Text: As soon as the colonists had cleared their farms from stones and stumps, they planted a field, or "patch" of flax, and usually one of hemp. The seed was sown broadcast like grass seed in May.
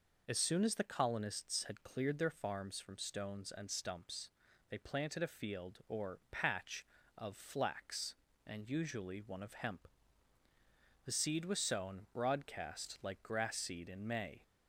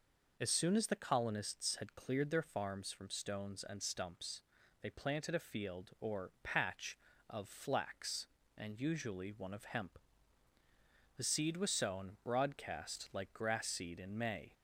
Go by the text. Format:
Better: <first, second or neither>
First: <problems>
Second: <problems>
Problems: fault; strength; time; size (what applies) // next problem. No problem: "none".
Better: neither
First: none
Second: none